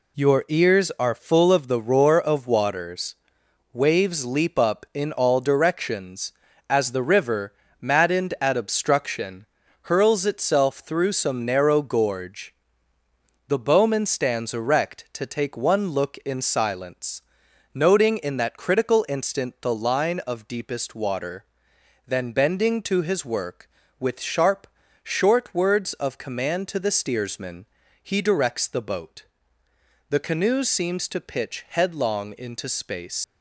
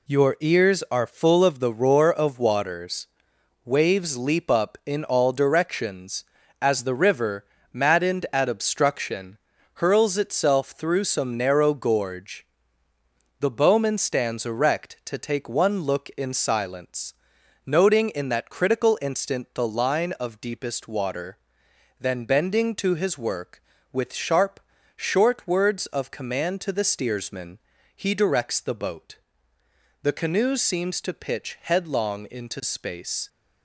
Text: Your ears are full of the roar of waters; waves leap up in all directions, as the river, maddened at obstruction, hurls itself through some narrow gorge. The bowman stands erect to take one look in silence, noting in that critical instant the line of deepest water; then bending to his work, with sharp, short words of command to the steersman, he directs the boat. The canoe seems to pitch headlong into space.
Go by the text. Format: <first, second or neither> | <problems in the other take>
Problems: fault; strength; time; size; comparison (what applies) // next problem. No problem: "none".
second | leaves "space" unfinished; at 33.2 s; 90 ms